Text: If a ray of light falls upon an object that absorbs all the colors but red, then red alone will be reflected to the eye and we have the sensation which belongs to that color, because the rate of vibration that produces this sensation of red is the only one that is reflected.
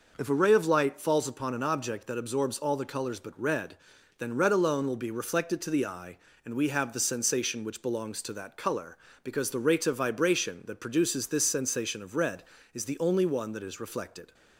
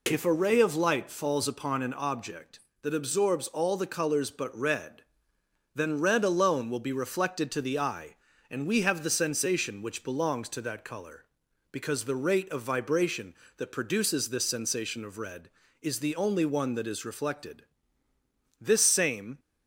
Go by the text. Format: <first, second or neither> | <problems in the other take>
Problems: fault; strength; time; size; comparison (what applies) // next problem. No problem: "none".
first | goes on to say "This same"; noticeable; from 18.6 s on; 0.78 s long